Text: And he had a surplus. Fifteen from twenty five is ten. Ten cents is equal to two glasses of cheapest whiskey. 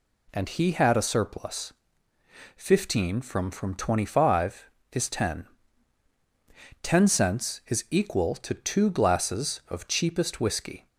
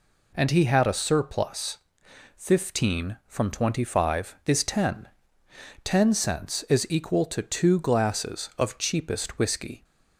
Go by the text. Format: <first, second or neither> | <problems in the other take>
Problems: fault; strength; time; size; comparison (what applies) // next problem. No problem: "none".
second | says "from" twice; at 3.5 s